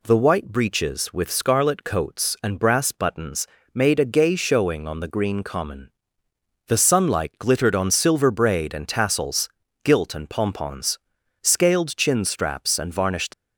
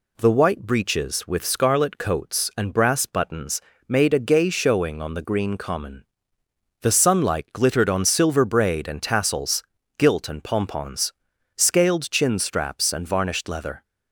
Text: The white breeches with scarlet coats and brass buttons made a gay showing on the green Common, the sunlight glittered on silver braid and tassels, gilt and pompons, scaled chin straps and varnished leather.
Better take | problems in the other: second | pauses between "buttons" and "made"; slight; at 3.4 s; 0.30 s long; slight in the second // stops before "leather"; at 13.3 s

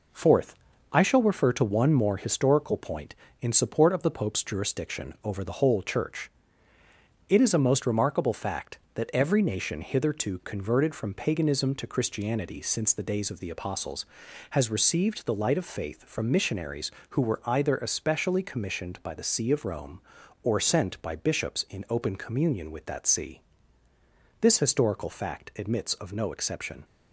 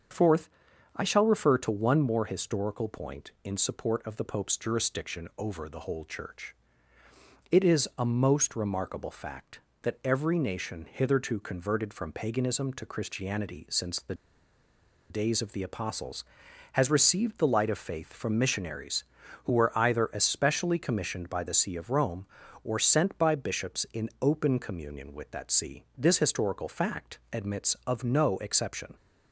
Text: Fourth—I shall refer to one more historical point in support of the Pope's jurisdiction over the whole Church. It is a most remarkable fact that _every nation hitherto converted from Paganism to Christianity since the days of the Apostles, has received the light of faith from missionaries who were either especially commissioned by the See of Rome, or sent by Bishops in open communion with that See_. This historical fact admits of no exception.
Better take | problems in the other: first | starts louder than the rest; until 1.5 s; 7 dB // pauses between "the" and "days"; noticeable; at 14.1 s; 0.96 s long

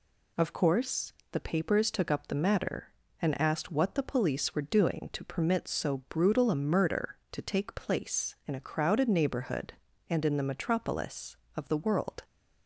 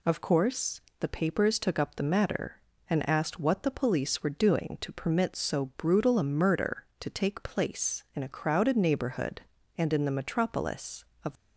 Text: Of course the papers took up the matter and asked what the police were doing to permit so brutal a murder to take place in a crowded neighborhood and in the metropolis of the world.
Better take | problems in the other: first | pauses between "course" and "the"; slight; at 0.8 s; 0.20 s long; slight in the first // stops before "the world"; at 11.3 s

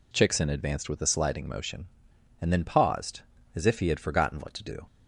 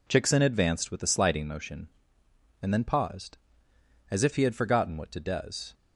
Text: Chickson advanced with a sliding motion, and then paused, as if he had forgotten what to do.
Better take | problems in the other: first | says "does" for "do"; at 5.1 s

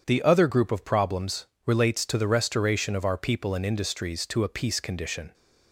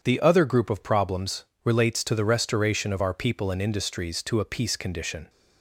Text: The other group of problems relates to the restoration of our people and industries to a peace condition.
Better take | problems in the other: neither | starts louder than the rest; strong; the same in both // pauses between "problems" and "relates"; slight; the same in both

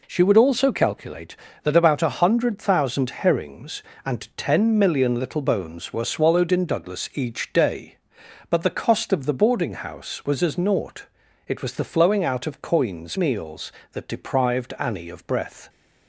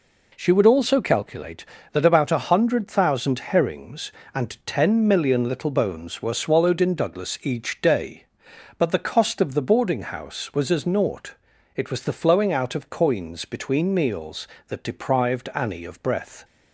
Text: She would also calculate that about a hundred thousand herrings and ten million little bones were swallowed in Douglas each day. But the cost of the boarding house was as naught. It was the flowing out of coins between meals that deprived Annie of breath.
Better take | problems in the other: second | skips "between"; at 13.1 s

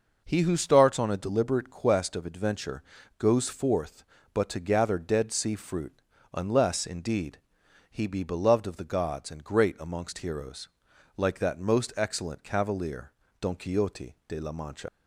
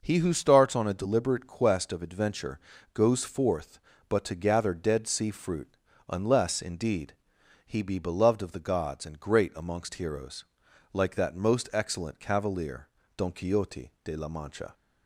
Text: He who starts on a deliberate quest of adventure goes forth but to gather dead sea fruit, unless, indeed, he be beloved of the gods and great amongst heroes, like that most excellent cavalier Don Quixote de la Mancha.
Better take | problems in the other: second | pauses between "adventure" and "goes"; slight; at 2.8 s; 0.36 s long; slight in the second // pauses between "cavalier" and "Don"; slight; at 13.1 s; 0.30 s long; slight in the second // leaves "Mancha" unfinished; at 14.8 s; 85 ms

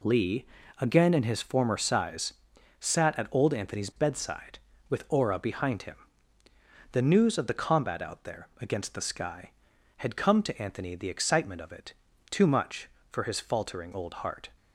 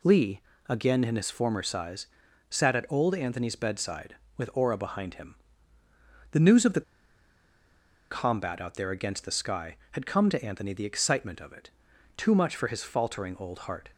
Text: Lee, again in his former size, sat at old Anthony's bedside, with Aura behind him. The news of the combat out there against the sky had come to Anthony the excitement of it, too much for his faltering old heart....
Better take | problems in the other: first | pauses between "the" and "combat"; strong; at 6.8 s; 1.2 s long

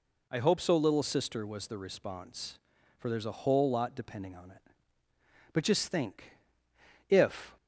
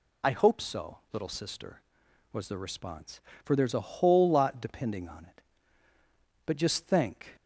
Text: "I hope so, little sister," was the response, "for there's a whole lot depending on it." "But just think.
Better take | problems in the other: second | goes on to say "If"; slight; from 7.0 s on; 0.48 s long

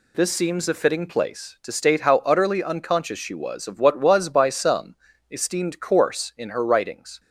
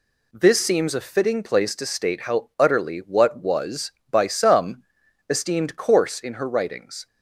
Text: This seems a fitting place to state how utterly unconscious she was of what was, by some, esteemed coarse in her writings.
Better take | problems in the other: first | skips "unconscious she was of"; at 2.9 s

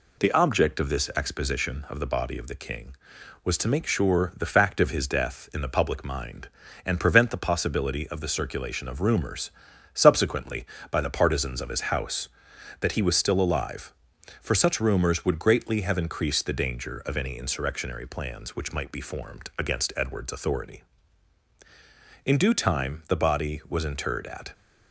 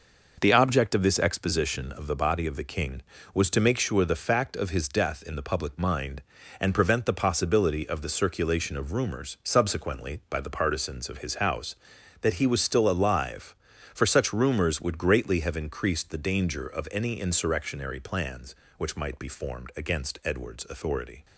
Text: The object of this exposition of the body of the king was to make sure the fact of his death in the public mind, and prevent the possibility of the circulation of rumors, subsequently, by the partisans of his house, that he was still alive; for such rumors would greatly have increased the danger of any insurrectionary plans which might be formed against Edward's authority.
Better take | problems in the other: second | goes on to say "In due time the body was interred at"; strong; from 22.2 s on; 2.2 s long

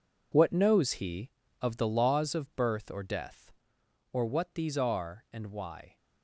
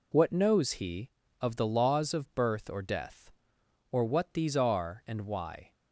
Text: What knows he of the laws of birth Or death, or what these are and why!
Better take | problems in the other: second | gets quieter; strong; throughout; 12.5 dB

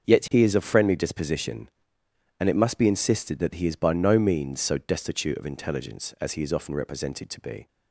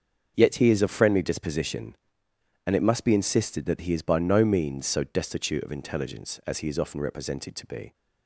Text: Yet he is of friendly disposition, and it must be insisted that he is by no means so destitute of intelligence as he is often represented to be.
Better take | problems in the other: neither | starts louder than the rest; the same in both

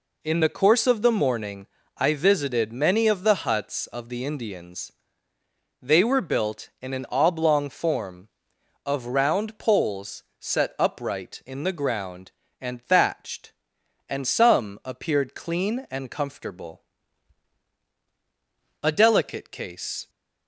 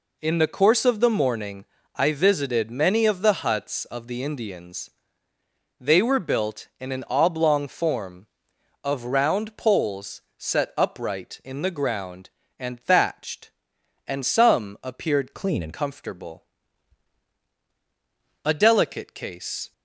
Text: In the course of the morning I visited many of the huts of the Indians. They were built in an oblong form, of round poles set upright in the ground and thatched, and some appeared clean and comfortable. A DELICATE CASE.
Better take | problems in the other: first | pauses between "morning" and "I"; slight; at 1.6 s; 0.30 s long; slight in the first // pauses between "poles" and "set"; slight; at 10.2 s; 0.16 s long; slight in the first // changes voice from "clean" to "and"; from 15.3 to 15.7 s; 0.4 s long

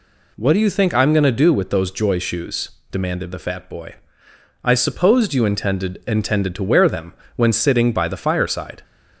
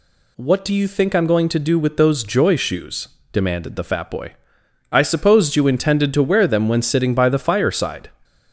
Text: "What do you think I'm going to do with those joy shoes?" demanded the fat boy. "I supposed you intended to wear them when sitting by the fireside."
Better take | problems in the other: second | says "intended" twice; at 6.0 s // pauses between "them" and "when"; slight; at 7.1 s; 0.24 s long

